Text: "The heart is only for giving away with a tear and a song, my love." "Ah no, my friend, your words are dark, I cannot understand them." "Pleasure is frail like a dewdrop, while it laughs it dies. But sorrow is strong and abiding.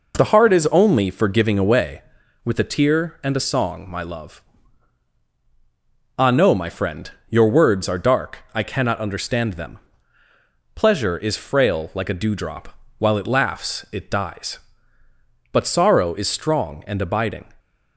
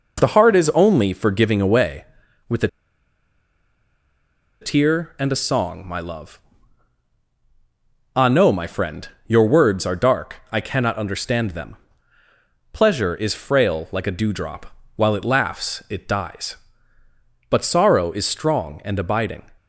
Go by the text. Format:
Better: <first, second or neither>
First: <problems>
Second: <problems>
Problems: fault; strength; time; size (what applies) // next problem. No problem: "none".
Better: first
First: none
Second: pauses between "a" and "tear"; strong; at 2.6 s; 1.9 s long